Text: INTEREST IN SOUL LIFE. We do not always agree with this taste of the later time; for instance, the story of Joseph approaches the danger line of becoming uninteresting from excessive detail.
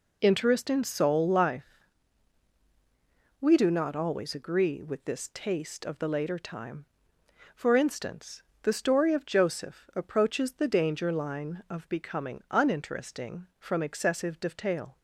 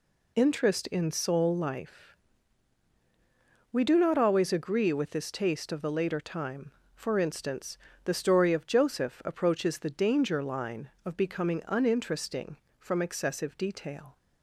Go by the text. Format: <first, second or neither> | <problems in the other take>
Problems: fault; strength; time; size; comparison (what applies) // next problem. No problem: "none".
neither | none